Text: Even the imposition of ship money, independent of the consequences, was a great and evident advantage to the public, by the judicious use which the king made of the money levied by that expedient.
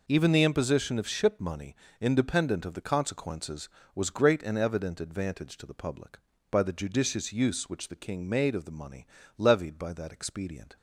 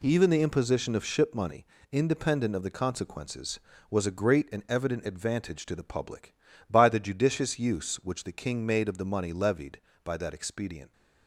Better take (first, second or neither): second